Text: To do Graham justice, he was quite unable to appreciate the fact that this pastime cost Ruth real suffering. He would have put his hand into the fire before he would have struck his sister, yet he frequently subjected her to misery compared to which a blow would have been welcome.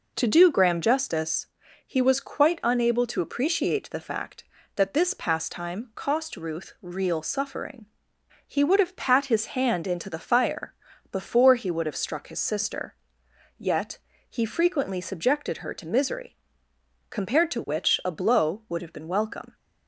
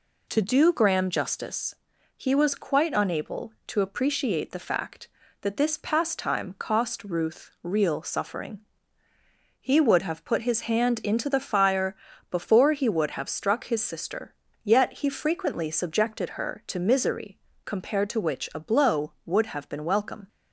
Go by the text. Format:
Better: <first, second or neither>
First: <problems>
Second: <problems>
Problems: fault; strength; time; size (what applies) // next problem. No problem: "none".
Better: second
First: says "pat" for "put"; at 8.9 s // pauses between "fire" and "before"; at 10.7 s; 0.38 s long // pauses between "yet" and "he"; slight; at 13.9 s; 0.32 s long // pauses between "misery" and "compared"; noticeable; at 16.3 s; 0.74 s long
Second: pauses between "fire" and "before"; slight; at 11.9 s; 0.34 s long // pauses between "misery" and "compared"; slight; at 17.3 s; 0.24 s long